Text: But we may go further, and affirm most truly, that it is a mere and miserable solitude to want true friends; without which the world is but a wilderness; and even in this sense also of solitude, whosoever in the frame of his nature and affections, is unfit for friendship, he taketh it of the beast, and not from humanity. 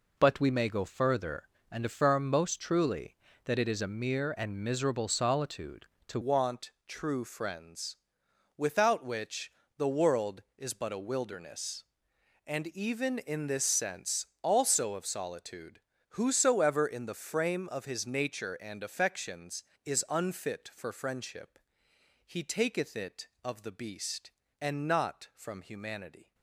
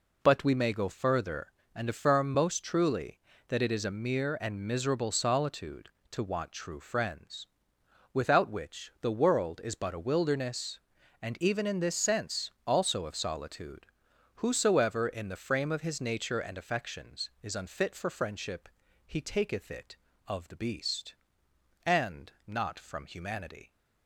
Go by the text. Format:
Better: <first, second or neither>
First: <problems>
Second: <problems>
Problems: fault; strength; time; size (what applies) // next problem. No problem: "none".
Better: second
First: changes voice at "want"; from 6.2 s on; 20.1 s long // pauses between "want" and "true"; slight; at 6.7 s; 0.16 s long // pauses between "which" and "the"; slight; at 9.5 s; 0.26 s long // pauses between "sense" and "also"; slight; at 14.2 s; 0.16 s long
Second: pauses between "sense" and "also"; slight; at 12.5 s; 0.16 s long